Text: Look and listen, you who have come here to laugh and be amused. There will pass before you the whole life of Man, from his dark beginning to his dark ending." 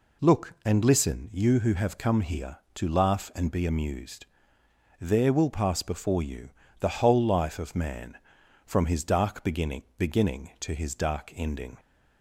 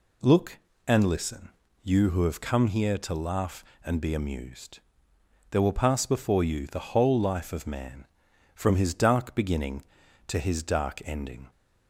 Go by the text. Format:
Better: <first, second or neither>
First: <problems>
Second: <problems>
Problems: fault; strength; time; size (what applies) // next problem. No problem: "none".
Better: second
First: pauses between "you" and "the"; slight; at 6.4 s; 0.32 s long // says "beginning" twice; at 9.9 s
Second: none